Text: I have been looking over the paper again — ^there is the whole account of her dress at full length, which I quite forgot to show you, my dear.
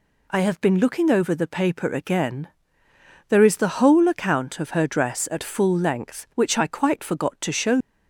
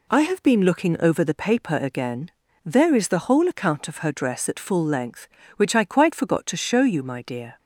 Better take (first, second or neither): second